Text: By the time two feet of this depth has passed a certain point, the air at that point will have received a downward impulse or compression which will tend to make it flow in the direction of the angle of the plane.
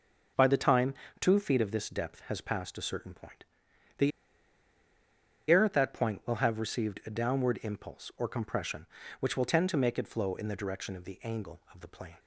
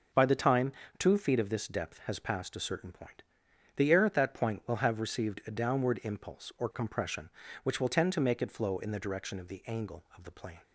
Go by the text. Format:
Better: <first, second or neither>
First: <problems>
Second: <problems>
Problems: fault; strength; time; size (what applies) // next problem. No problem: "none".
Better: second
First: starts louder than the rest; noticeable; until 1.6 s; 6 dB // pauses between "time" and "two"; slight; at 0.9 s; 0.28 s long // pauses between "the" and "air"; strong; at 4.1 s; 1.4 s long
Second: pauses between "time" and "two"; slight; at 0.7 s; 0.28 s long